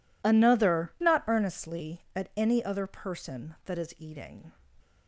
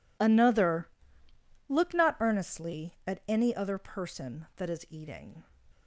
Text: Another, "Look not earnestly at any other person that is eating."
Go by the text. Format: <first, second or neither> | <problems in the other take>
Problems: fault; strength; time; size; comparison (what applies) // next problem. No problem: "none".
second | skips "Look"; at 0.9 s